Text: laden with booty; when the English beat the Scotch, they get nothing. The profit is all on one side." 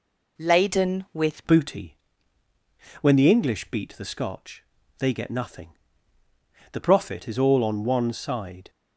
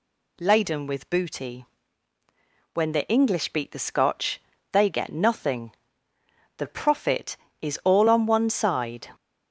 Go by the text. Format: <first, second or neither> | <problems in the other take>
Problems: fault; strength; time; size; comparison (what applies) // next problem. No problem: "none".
second | changes voice at "booty"; from 1.4 s on; 7.2 s long